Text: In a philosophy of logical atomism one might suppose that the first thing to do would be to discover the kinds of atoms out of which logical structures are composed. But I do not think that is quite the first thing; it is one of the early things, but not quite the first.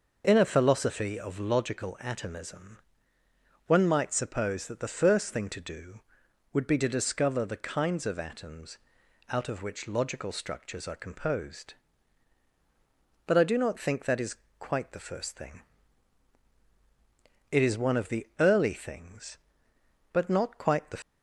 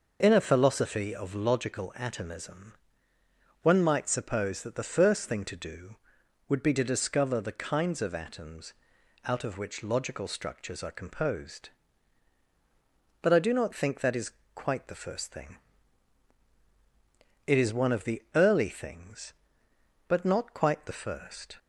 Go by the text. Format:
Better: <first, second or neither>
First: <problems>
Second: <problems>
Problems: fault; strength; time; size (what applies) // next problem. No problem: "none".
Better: second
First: pauses between "atomism" and "one"; noticeable; at 2.7 s; 0.90 s long // pauses between "atoms" and "out"; noticeable; at 8.7 s; 0.52 s long // pauses between "is" and "quite"; slight; at 14.3 s; 0.24 s long // stops before "first"; at 21.0 s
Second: pauses between "atomism" and "one"; noticeable; at 2.7 s; 0.90 s long // pauses between "atoms" and "out"; noticeable; at 8.7 s; 0.52 s long // pauses between "is" and "quite"; slight; at 14.2 s; 0.24 s long